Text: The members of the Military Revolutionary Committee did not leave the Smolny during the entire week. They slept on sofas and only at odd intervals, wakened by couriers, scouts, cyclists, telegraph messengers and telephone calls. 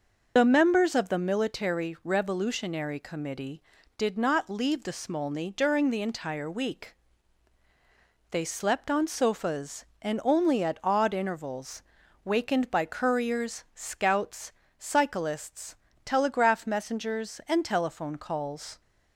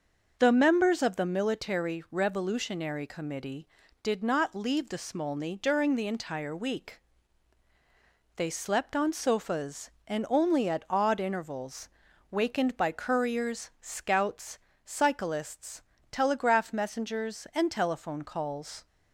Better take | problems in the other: second | loses the start of "The"; at 0.3 s; 45 ms

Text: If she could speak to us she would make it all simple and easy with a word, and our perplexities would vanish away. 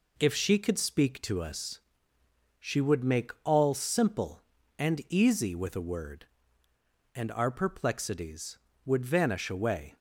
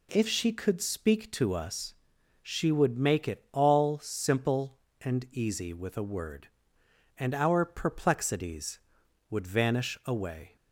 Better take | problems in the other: second | pauses between "us" and "she"; noticeable; at 1.7 s; 0.80 s long; noticeable in the second // skips "it"; at 3.3 s

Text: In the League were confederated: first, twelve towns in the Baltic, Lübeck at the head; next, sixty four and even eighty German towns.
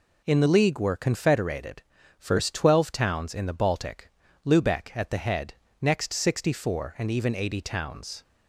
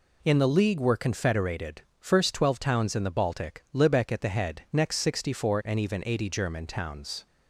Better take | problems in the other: second | skips "German"; at 7.6 s

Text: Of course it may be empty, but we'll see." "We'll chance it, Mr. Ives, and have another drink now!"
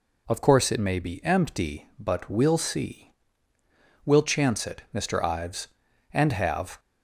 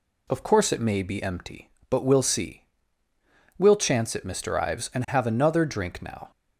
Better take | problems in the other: second | stops before "another drink now"; at 6.7 s

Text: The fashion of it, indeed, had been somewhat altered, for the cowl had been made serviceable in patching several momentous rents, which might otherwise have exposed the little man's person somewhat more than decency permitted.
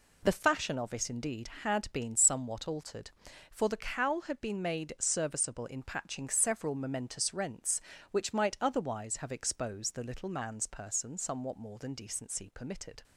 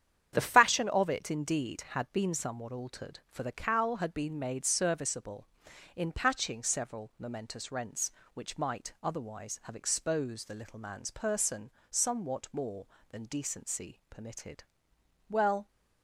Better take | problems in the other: first | starts louder than the rest; strong; until 1.3 s; 9 dB // pauses between "person" and "somewhat"; slight; at 11.7 s; 0.18 s long // goes on to say "Well"; slight; from 15.2 s on; 0.38 s long

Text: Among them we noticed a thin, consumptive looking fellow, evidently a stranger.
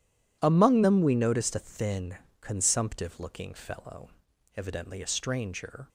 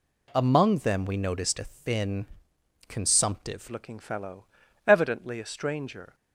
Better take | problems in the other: first | changes voice at "looking"; from 3.7 s on; 2.4 s long

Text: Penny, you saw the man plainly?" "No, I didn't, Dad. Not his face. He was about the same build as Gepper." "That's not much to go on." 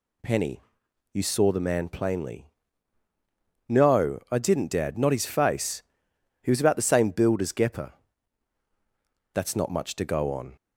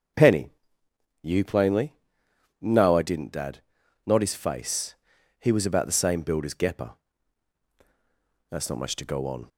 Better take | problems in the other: first | starts louder than the rest; until 1.8 s; 7 dB // skips "saw the man"; at 1.4 s

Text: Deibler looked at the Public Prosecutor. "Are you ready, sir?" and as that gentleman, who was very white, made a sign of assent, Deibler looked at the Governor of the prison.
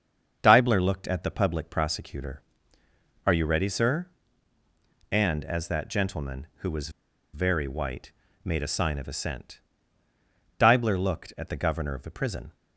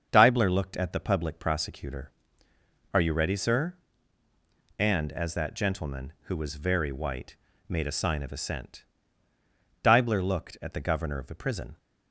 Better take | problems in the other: second | starts louder than the rest; strong; until 1.4 s; 7 dB; strong in the second // pauses between "was" and "very"; at 6.8 s; 0.44 s long

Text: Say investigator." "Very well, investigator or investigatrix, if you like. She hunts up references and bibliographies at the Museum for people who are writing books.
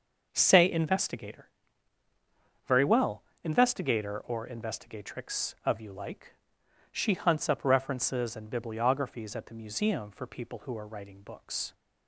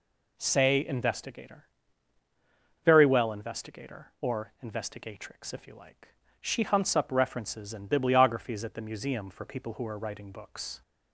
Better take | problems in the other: second | says "of" for "if"; at 5.6 s

